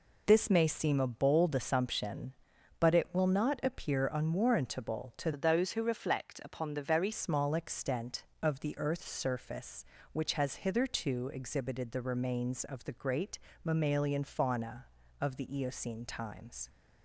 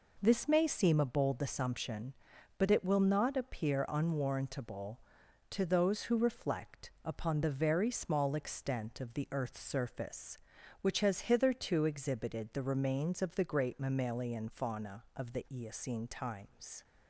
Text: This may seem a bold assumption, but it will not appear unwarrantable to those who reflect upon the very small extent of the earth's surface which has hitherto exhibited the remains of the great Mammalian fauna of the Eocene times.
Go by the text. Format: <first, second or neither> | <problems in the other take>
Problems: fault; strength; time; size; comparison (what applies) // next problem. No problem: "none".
second | changes voice from "those" to "very"; from 5.3 to 7.1 s; 1.8 s long // pauses between "great" and "Mammalian"; slight; at 13.3 s; 0.24 s long